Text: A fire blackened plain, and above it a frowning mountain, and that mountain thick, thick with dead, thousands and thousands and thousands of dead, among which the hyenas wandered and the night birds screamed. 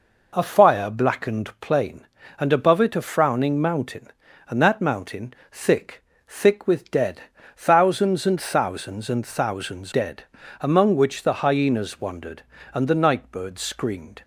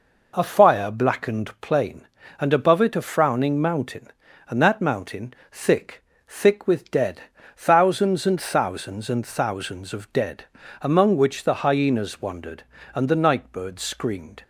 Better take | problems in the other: second | pauses between "mountain" and "thick"; slight; at 5.3 s; 0.20 s long; slight in the second // skips "of"; at 9.9 s

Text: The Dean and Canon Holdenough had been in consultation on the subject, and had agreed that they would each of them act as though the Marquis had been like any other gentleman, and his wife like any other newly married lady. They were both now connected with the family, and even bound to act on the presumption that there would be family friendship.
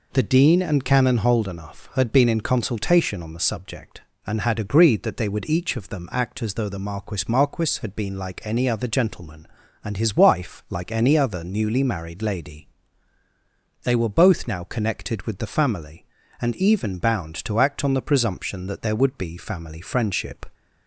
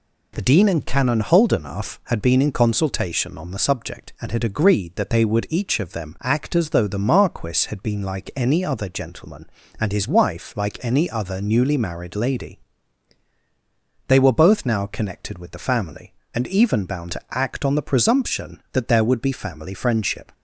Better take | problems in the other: second | says "Marquis" twice; at 7.2 s

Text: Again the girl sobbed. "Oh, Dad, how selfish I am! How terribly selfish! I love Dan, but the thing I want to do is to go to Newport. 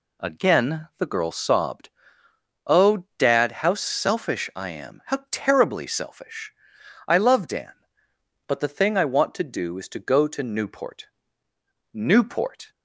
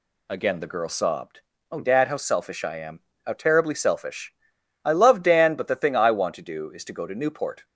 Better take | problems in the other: second | says "Newport" twice; at 11.9 s

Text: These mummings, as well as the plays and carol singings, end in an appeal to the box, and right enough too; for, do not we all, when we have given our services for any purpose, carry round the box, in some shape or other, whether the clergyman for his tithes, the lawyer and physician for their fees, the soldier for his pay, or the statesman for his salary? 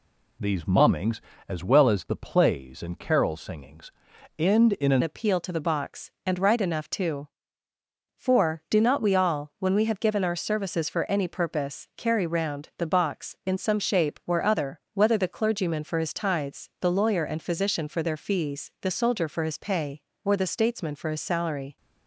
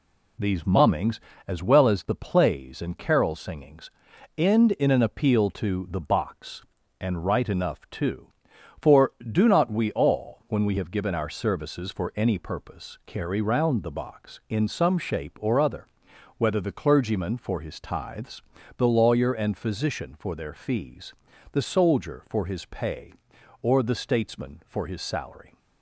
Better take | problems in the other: second | changes voice at "appeal"; from 5.0 s on; 16.7 s long

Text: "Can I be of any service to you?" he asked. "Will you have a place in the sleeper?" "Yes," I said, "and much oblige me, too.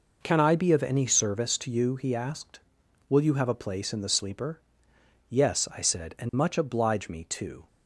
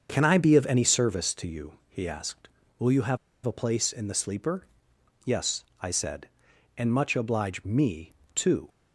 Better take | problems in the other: first | starts louder than the rest; until 1.1 s; 7 dB // pauses between "have" and "a"; slight; at 3.1 s; 0.28 s long

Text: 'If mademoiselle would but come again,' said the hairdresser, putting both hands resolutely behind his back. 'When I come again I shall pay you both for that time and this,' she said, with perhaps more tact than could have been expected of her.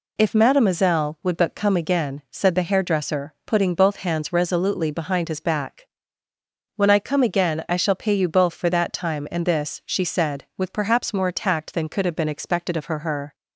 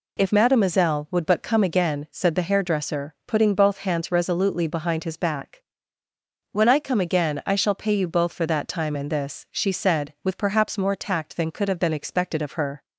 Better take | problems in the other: second | says "her" twice; at 12.9 s

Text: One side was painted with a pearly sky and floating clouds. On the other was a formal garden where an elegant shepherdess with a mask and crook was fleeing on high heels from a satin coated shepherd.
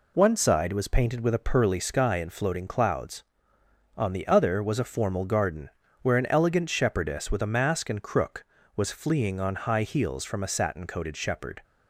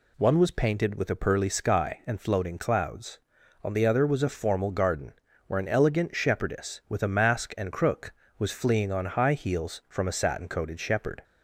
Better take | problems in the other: first | skips "side"; at 0.3 s // pauses between "garden" and "where"; slight; at 5.1 s; 0.36 s long; slight in the first

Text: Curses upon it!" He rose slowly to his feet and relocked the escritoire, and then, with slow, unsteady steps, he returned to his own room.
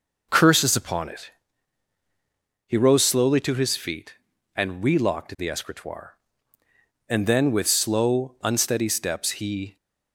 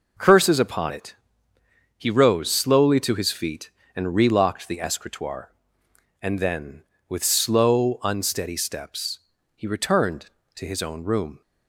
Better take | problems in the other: second | stops before "returned to his own room"; at 9.7 s

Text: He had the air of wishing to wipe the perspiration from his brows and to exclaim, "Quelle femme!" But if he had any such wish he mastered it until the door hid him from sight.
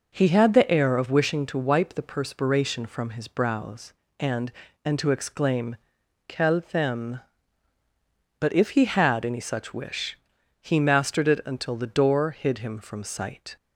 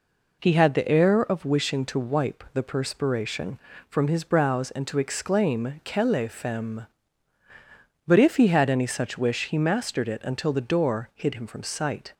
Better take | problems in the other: second | says "and" twice; at 4.8 s // pauses between "wish" and "he"; noticeable; at 10.1 s; 0.46 s long

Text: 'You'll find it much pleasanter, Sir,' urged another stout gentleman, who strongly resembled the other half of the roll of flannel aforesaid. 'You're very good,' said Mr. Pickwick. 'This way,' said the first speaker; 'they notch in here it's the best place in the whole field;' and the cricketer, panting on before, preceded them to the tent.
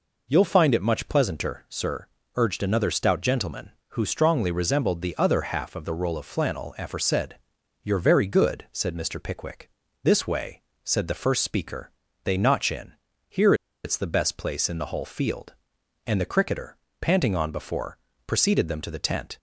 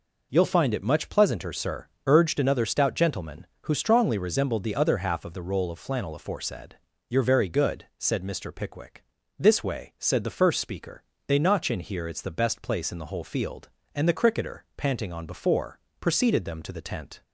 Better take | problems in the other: second | pauses between "in" and "here"; at 12.9 s; 0.38 s long // pauses between "here" and "it's"; slight; at 13.5 s; 0.30 s long

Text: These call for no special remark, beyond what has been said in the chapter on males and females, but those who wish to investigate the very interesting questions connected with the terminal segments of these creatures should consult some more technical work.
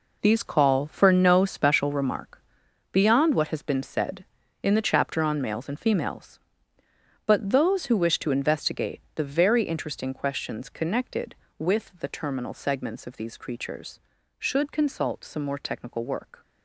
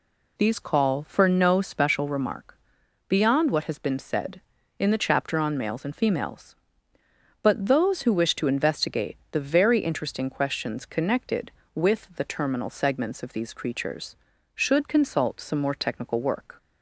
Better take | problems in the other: second | gets quieter; strong; throughout; 11 dB

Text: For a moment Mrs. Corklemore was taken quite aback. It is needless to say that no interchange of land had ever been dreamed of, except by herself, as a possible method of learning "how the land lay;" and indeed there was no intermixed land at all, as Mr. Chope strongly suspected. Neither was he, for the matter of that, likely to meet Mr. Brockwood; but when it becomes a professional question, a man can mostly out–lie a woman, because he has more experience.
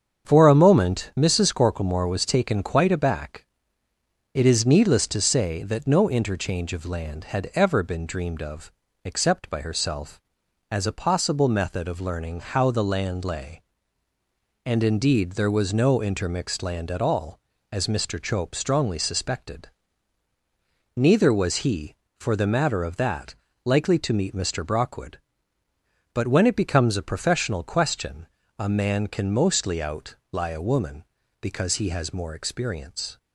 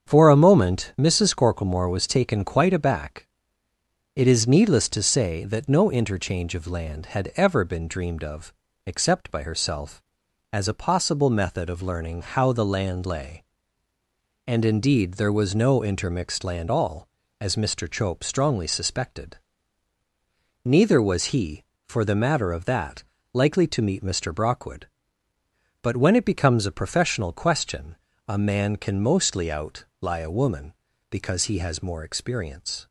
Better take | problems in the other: first | starts louder than the rest; strong; until 1.1 s; 7.5 dB; strong in the first // skips "at"; at 16.7 s

